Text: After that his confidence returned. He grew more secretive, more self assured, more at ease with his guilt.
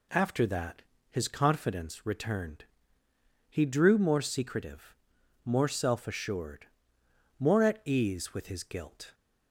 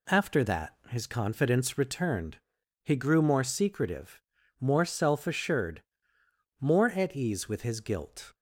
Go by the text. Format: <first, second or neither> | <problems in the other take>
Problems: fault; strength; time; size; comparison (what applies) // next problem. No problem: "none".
second | pauses between "that" and "his"; slight; at 0.8 s; 0.28 s long // says "drew" for "grew"; at 3.6 s